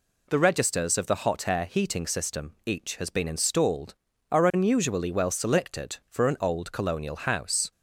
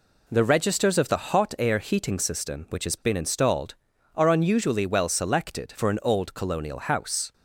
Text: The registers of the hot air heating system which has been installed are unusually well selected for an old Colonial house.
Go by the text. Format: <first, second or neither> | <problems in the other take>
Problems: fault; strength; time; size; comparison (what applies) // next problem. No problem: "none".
second | says "each" for "which"; at 2.6 s